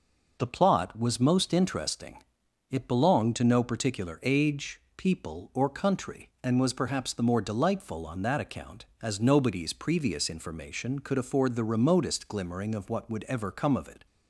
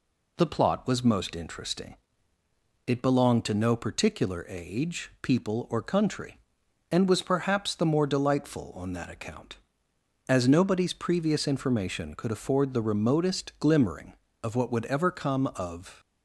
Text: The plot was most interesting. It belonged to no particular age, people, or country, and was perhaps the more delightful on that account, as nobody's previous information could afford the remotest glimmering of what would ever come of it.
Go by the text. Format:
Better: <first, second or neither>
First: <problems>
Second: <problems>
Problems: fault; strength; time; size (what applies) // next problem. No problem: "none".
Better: first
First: none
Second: stops before "it"; at 15.9 s